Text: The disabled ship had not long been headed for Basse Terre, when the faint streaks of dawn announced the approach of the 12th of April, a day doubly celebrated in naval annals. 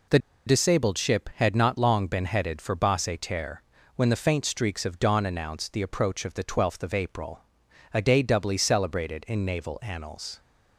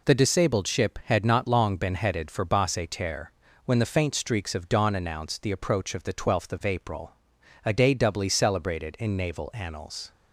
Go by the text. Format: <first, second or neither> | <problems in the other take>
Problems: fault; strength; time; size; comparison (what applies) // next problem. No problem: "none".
second | pauses between "The" and "disabled"; slight; at 0.1 s; 0.28 s long